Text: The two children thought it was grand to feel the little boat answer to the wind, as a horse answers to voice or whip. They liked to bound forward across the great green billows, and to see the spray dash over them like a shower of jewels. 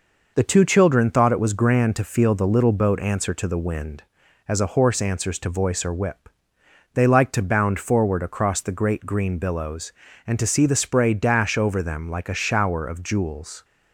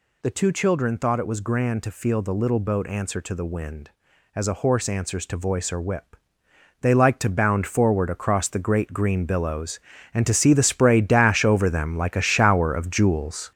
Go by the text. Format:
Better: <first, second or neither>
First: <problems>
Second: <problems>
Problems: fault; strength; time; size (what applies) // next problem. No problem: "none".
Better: first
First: none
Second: gets louder; throughout; 6.5 dB